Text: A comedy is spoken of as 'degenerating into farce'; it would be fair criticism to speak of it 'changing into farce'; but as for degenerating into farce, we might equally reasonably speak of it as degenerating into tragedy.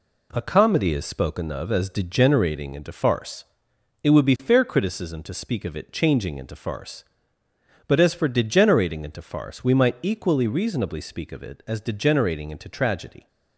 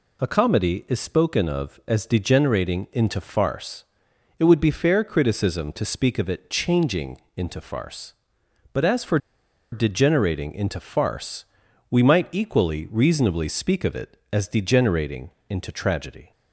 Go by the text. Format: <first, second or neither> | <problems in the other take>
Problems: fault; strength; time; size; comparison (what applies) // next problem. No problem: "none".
first | pauses between "changing" and "into"; slight; at 7.2 s; 0.16 s long // pauses between "for" and "degenerating"; noticeable; at 9.1 s; 0.54 s long // pauses between "degenerating" and "into"; slight; at 15.3 s; 0.18 s long